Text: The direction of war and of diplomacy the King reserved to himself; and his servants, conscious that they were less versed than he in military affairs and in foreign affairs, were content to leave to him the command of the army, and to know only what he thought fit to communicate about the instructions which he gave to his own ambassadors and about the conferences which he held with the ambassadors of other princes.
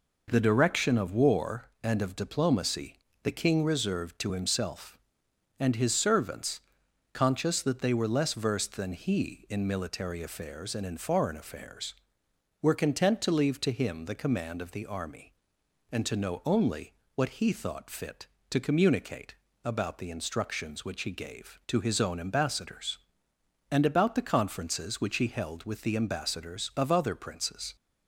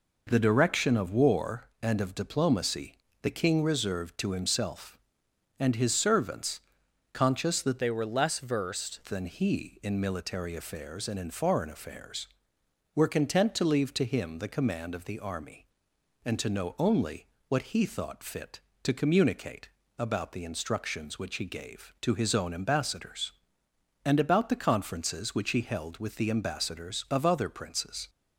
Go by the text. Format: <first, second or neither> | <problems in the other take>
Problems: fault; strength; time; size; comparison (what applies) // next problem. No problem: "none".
first | pauses between "diplomacy" and "the"; slight; at 2.9 s; 0.26 s long; slight in the first // changes voice from "they" to "versed"; from 7.7 to 8.9 s; 1.2 s long // pauses between "only" and "what"; slight; at 17.2 s; 0.22 s long; slight in the first // pauses between "communicate" and "about"; slight; at 19.6 s; 0.28 s long; slight in the first